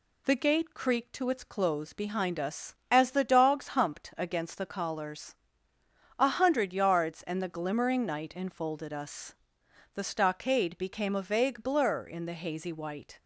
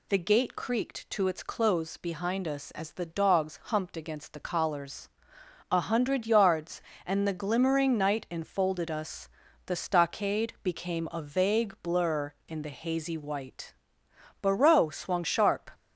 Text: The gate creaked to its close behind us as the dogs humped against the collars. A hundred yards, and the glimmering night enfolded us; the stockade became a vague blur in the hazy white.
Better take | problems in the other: first | goes on to say "Barreau swung sharp"; noticeable; from 14.4 s on; 1.2 s long

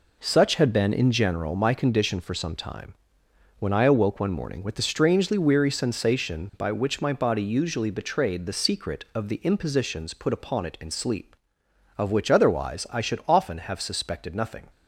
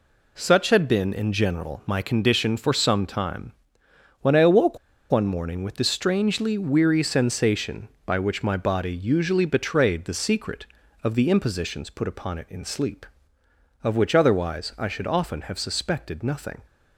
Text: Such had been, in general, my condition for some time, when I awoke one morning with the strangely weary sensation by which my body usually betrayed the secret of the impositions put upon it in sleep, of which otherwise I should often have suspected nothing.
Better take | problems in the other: first | pauses between "awoke" and "one"; slight; at 4.7 s; 0.32 s long

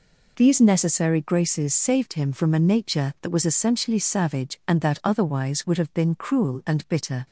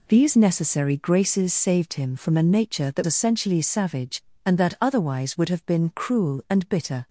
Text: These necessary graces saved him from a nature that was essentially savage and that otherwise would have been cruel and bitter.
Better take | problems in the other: first | skips "was"; at 3.0 s

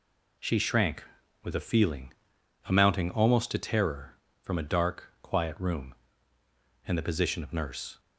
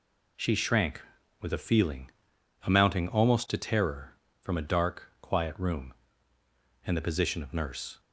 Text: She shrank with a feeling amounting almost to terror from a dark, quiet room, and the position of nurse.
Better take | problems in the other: neither | pauses between "feeling" and "amounting"; noticeable; the same in both

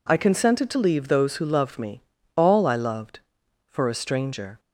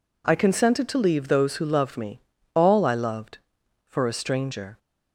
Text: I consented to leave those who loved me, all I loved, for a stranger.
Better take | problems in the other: neither | none

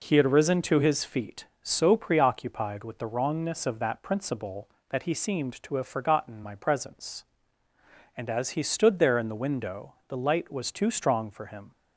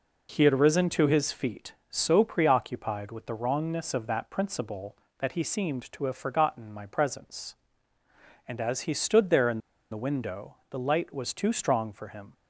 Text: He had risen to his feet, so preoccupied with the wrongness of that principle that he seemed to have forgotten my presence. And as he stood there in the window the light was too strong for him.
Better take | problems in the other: first | pauses between "in" and "the"; slight; at 9.5 s; 0.33 s long

